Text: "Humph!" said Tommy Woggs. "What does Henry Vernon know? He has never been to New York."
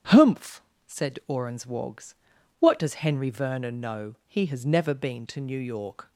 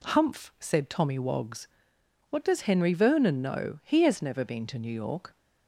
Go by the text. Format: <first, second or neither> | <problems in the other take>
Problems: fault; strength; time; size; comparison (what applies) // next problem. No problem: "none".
second | starts louder than the rest; strong; until 1.4 s; 8.5 dB // says "Orans" for "Tommy"; at 1.2 s